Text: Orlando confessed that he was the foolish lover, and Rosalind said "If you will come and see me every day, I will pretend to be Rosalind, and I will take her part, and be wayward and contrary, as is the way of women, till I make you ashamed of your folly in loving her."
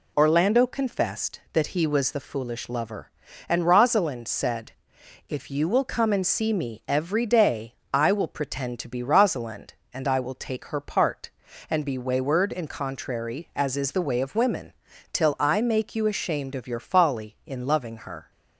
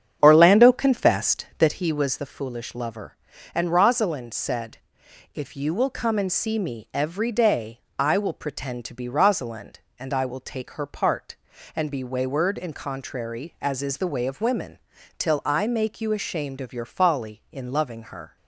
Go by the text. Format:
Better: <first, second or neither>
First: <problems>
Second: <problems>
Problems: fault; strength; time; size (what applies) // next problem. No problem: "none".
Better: first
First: pauses between "said" and "If"; noticeable; at 4.7 s; 0.56 s long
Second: starts louder than the rest; strong; until 1.7 s; 8 dB // pauses between "said" and "If"; noticeable; at 4.7 s; 0.56 s long